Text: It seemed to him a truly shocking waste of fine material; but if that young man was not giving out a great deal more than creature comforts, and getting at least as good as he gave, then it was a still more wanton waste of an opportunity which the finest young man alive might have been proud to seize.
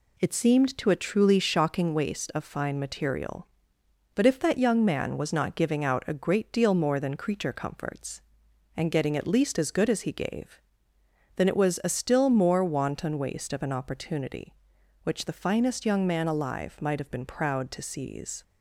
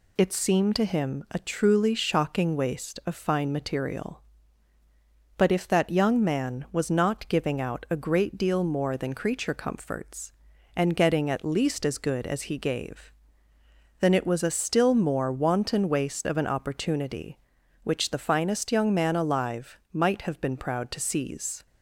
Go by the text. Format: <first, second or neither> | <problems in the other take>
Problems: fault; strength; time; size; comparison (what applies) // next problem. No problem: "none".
second | skips "him"; at 0.8 s